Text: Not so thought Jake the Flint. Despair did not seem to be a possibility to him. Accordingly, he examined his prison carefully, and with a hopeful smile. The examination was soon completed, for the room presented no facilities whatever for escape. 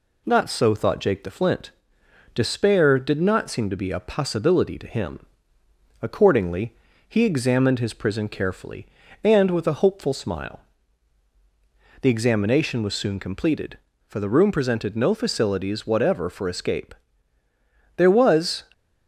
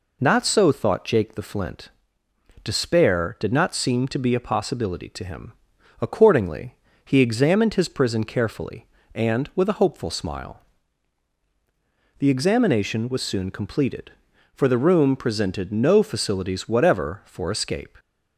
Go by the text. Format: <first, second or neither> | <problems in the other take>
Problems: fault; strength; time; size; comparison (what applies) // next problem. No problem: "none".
second | goes on to say "There was"; noticeable; from 17.9 s on; 0.66 s long